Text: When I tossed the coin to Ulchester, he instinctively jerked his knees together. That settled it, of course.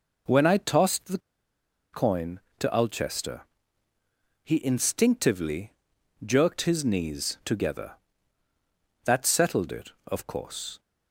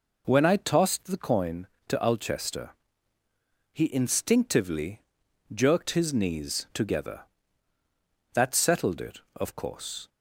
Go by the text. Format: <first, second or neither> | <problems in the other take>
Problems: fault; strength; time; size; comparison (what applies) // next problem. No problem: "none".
second | pauses between "the" and "coin"; noticeable; at 1.1 s; 0.72 s long // pauses between "instinctively" and "jerked"; noticeable; at 5.7 s; 0.54 s long; noticeable in the second